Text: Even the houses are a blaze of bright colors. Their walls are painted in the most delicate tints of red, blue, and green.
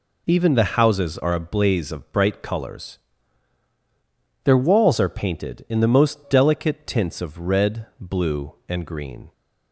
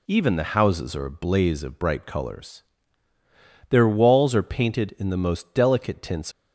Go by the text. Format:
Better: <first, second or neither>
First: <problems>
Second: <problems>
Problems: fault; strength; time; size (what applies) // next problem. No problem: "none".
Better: first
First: none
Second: stops before "of red blue and green"; at 6.3 s